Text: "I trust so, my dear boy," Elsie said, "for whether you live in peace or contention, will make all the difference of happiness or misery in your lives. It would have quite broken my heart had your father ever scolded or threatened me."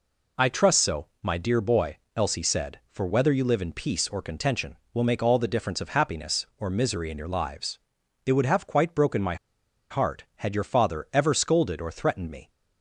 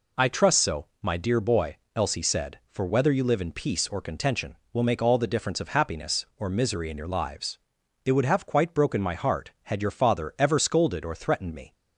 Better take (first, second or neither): second